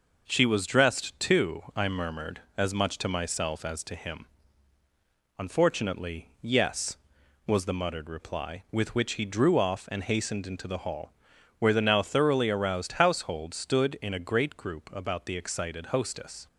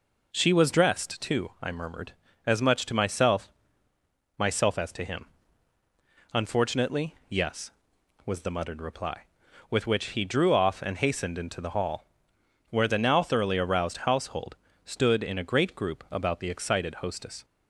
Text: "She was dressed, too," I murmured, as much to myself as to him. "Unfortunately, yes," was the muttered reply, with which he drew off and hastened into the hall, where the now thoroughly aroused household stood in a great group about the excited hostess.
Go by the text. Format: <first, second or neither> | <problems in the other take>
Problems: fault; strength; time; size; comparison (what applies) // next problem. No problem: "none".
first | says "myself" twice; at 4.3 s // pauses between "household" and "stood"; slight; at 14.5 s; 0.28 s long